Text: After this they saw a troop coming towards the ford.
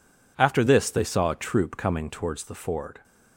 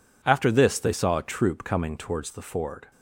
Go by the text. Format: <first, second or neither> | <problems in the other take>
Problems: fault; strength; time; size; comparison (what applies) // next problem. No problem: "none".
neither | none